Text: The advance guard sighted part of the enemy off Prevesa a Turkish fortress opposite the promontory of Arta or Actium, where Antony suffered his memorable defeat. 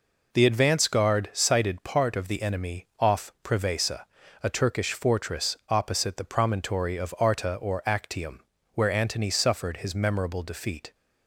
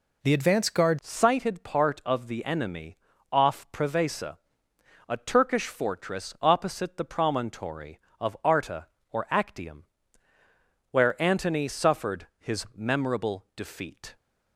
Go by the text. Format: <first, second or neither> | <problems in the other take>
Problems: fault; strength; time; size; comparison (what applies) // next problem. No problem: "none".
first | changes voice at "sighted"; from 1.0 s on; 13.1 s long // pauses between "enemy" and "off"; slight; at 2.9 s; 0.36 s long // pauses between "Prevesa" and "a"; noticeable; at 4.3 s; 0.70 s long; slight in the first